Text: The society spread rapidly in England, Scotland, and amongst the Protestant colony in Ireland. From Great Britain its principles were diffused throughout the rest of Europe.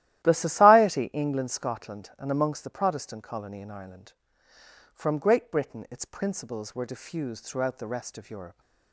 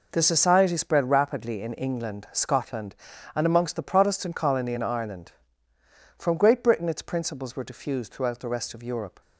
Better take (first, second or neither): second